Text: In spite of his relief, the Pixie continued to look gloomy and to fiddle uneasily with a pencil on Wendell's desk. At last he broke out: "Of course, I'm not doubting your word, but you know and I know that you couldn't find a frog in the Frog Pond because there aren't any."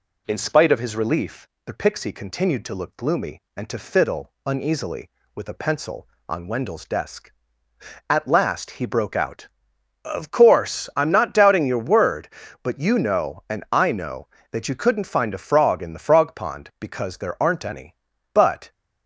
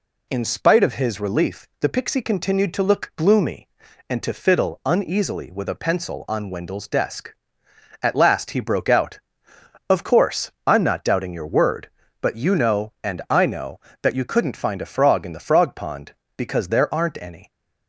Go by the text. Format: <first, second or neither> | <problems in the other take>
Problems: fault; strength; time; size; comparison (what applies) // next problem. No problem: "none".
second | goes on to say "But"; slight; from 18.3 s on; 0.38 s long